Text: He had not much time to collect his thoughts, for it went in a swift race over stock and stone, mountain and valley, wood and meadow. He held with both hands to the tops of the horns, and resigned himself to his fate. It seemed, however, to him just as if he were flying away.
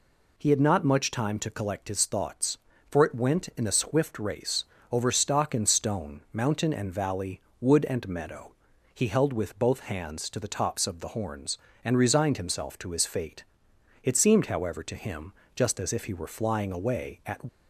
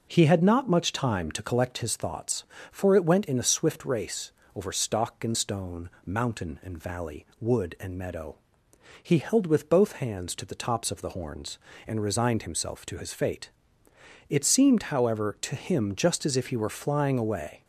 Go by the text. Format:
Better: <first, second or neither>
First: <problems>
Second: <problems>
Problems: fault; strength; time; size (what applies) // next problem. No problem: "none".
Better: second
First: pauses between "race" and "over"; slight; at 4.6 s; 0.26 s long // pauses between "him" and "just"; slight; at 15.3 s; 0.22 s long // goes on to say "At"; slight; from 17.2 s on; 0.14 s long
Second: pauses between "race" and "over"; slight; at 4.3 s; 0.24 s long